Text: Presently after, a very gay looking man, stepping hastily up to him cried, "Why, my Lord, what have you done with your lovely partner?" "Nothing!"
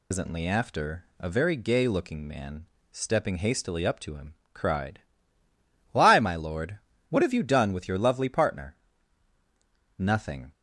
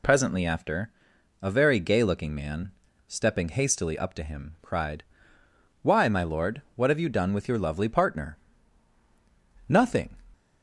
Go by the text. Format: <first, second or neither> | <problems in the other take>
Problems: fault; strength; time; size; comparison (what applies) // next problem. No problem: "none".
second | loses the start of "Presently"; at 0.1 s; 140 ms // pauses between "him" and "cried"; slight; at 4.3 s; 0.18 s long